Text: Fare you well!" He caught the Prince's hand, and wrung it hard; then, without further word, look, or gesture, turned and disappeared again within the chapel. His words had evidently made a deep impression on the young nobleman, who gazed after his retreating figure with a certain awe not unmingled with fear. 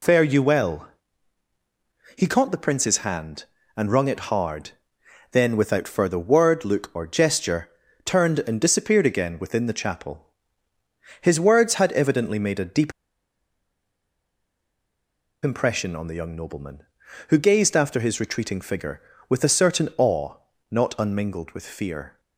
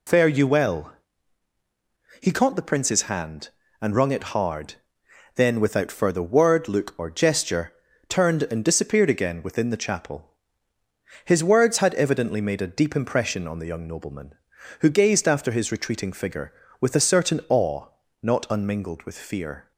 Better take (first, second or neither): second